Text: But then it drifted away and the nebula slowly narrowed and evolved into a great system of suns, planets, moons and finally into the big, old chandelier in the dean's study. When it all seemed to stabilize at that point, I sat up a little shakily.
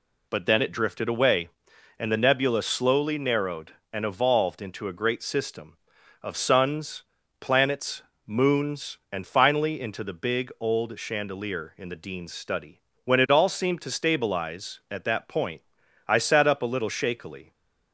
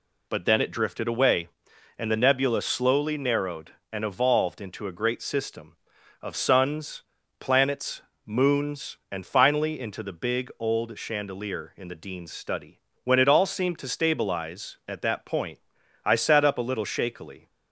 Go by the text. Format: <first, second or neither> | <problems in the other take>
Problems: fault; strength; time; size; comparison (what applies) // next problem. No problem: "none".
neither | none